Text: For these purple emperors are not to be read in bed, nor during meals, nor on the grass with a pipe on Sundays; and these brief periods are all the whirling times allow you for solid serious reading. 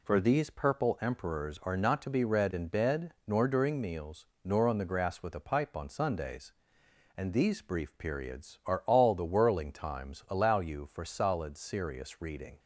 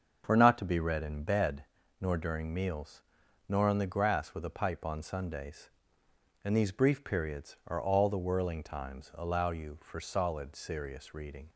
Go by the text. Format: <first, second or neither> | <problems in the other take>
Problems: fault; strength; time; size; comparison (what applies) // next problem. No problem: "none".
first | starts louder than the rest; until 1.2 s; 7 dB // skips "these purple emperors are"; at 0.3 s